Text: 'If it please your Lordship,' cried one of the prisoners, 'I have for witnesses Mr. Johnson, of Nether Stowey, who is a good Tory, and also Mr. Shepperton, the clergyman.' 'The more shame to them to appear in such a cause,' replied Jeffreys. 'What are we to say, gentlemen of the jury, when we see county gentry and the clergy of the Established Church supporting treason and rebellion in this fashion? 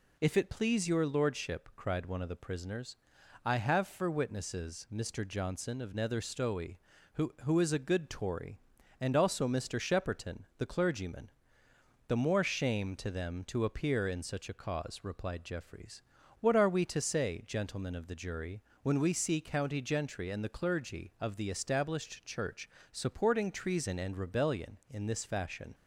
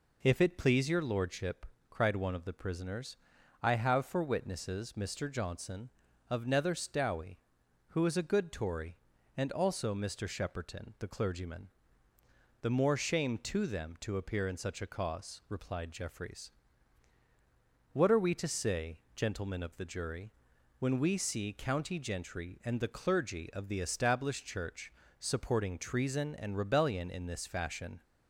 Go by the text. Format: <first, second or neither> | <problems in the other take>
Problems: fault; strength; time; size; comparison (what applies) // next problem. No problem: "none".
second | says "who" twice; at 7.4 s // pauses between "Church" and "supporting"; slight; at 22.6 s; 0.22 s long; slight in the second